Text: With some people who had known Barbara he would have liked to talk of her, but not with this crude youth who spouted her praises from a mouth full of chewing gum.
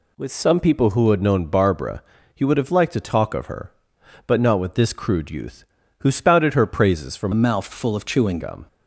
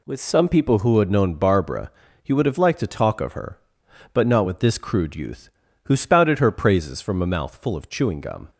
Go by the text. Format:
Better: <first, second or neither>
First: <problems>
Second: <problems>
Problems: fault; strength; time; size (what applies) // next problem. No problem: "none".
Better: second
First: pauses between "Barbara" and "he"; slight; at 2.0 s; 0.32 s long // changes voice from "a" to "chewing"; from 7.3 to 8.3 s; 1.0 s long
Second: pauses between "Barbara" and "he"; slight; at 1.8 s; 0.32 s long